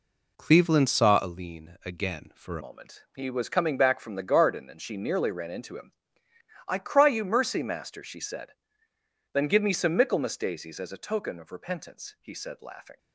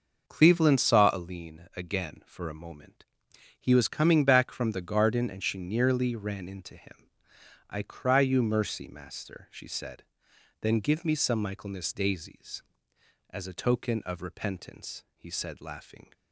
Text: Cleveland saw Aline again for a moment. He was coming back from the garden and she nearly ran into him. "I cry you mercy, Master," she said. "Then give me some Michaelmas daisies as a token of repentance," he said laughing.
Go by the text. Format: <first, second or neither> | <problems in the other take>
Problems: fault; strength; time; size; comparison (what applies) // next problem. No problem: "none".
second | changes voice at "moment"; from 2.5 s on; 10.4 s long